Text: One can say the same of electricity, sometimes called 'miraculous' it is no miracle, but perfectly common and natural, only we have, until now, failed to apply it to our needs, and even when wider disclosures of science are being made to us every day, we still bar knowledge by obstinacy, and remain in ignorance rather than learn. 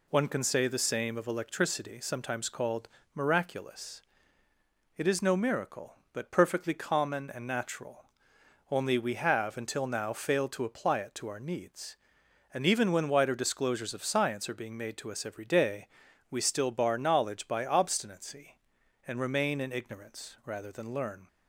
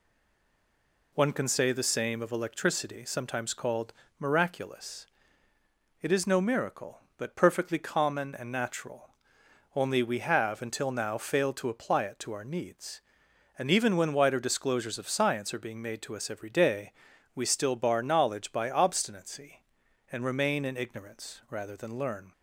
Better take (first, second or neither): first